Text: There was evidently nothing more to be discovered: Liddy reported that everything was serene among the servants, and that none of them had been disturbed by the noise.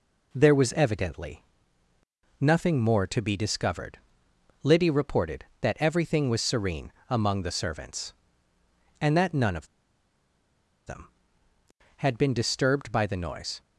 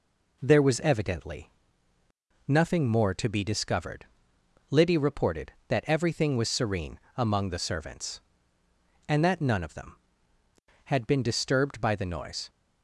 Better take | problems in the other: second | pauses between "evidently" and "nothing"; noticeable; at 1.4 s; 0.96 s long; noticeable in the second // pauses between "serene" and "among"; slight; at 6.9 s; 0.16 s long; slight in the second // pauses between "of" and "them"; at 9.6 s; 1.1 s long

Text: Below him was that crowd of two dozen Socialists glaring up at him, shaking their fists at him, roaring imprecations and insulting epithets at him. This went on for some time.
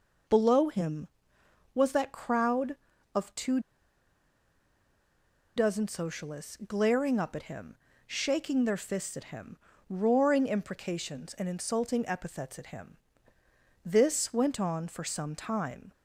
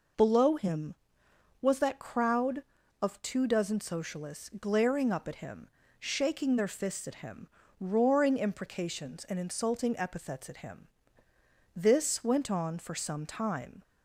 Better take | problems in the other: second | pauses between "two" and "dozen"; strong; at 3.5 s; 1.9 s long

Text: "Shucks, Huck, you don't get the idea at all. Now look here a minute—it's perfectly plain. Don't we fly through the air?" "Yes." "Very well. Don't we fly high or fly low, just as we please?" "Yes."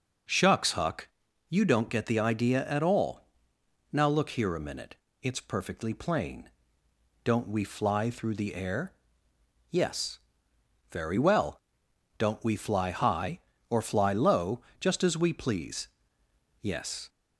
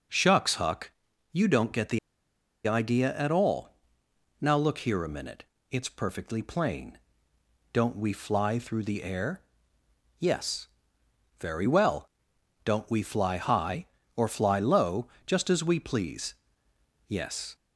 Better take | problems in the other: first | pauses between "the" and "idea"; noticeable; at 1.9 s; 0.68 s long

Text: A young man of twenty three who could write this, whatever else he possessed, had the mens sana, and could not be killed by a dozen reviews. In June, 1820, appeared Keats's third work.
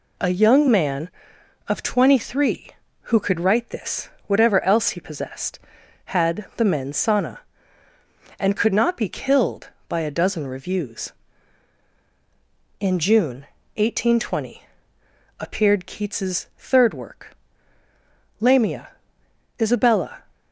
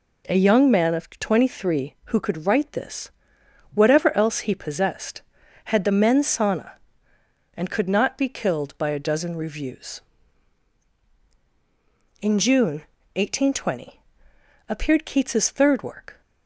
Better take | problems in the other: second | goes on to say "Lamia Isabella"; strong; from 18.4 s on; 1.8 s long

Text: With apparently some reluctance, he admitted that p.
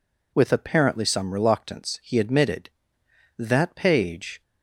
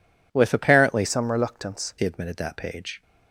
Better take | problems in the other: first | changes voice from "some" to "reluctance"; from 1.0 to 1.9 s; 0.9 s long

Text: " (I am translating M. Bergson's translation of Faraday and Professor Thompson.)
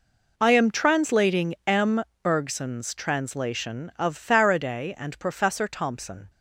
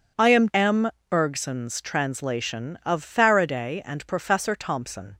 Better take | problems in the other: first | skips "translating"; at 0.4 s

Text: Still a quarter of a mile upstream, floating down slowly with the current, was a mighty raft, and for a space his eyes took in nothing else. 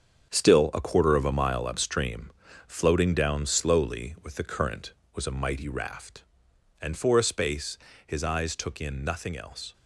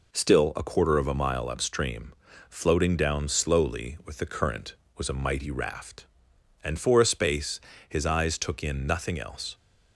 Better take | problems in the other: second | gets quieter; strong; throughout; 9 dB // pauses between "space" and "his"; slight; at 7.7 s; 0.28 s long; slight in the second

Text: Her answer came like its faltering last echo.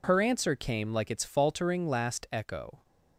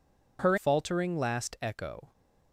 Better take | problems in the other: first | skips "answer came like its"; at 0.5 s

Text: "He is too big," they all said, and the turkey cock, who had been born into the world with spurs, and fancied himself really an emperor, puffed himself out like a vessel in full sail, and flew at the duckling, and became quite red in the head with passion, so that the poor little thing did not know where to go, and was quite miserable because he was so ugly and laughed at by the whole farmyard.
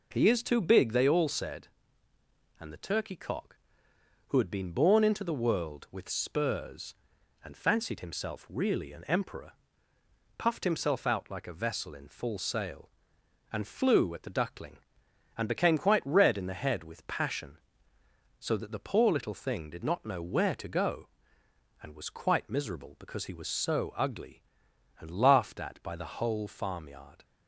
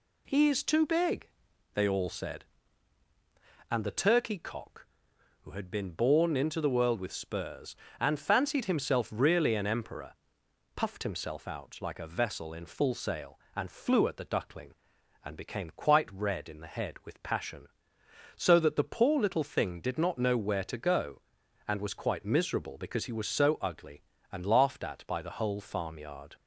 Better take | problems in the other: neither | none

